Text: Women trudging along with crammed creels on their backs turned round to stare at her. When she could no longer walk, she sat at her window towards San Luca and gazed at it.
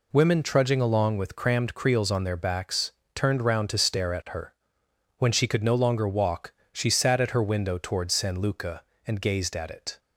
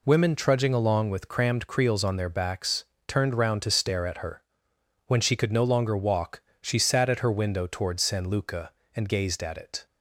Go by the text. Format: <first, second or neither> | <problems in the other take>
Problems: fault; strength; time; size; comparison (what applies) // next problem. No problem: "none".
neither | pauses between "backs" and "turned"; slight; the same in both